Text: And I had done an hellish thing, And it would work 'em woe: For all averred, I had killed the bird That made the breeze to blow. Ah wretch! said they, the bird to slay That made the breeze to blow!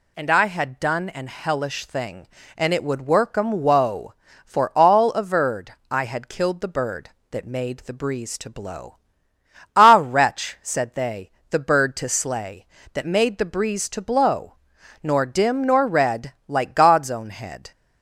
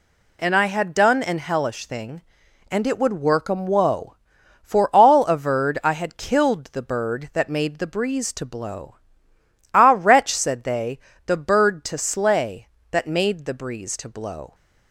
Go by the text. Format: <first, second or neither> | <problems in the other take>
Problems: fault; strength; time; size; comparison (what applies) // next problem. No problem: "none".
second | goes on to say "Nor dim nor red like God's own head"; strong; from 15.0 s on; 2.7 s long